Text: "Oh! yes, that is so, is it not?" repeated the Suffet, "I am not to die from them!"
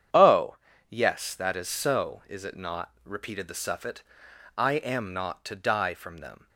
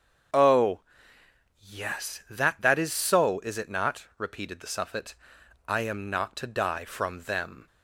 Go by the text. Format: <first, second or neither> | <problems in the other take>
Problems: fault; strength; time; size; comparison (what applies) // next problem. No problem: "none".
first | starts louder than the rest; strong; until 2.1 s; 7.5 dB; strong in the first // says "that" twice; at 2.6 s